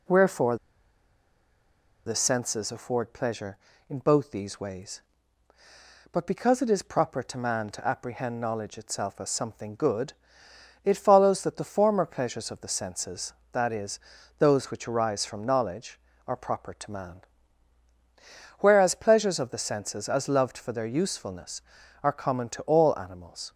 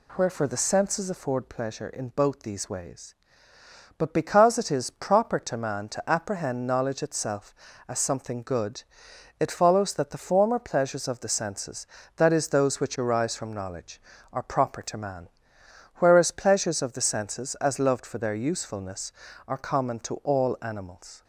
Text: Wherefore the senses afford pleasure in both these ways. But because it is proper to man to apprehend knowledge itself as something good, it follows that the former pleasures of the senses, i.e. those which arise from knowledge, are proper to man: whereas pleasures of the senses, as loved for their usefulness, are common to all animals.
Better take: second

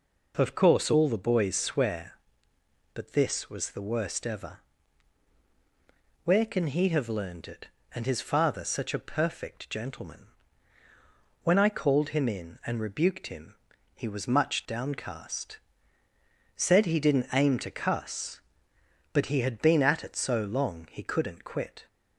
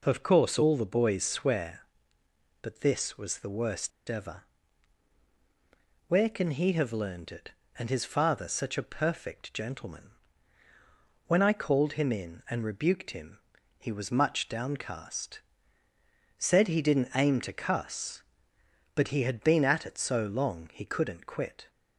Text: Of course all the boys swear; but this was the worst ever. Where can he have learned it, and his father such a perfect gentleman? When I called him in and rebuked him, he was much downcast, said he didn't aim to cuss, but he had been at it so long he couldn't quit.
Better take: first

